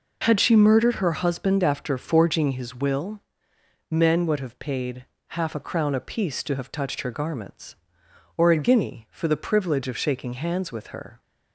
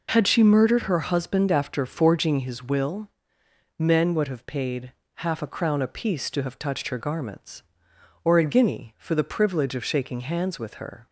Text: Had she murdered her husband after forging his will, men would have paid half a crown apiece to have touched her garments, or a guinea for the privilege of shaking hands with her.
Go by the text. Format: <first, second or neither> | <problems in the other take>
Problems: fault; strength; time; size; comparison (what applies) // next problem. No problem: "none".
neither | pauses between "paid" and "half"; slight; the same in both